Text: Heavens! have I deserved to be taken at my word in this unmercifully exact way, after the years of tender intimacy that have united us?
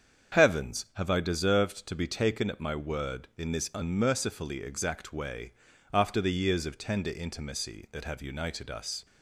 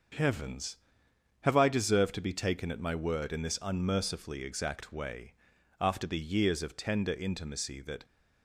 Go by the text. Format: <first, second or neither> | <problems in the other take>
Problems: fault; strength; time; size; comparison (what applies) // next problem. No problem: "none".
first | starts louder than the rest; until 1.8 s; 6.5 dB; strong in the first // stops before "have united us"; at 8.0 s